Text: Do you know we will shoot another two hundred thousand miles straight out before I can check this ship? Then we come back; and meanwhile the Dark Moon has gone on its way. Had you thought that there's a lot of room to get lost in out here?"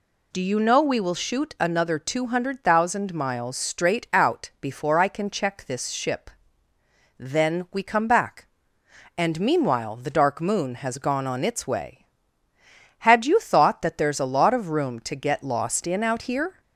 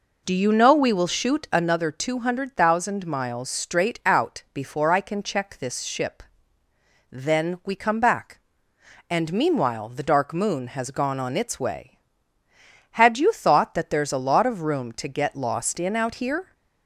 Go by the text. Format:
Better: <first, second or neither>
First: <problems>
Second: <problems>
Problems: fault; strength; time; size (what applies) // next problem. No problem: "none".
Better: first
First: none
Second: starts louder than the rest; noticeable; until 1.9 s; 4.5 dB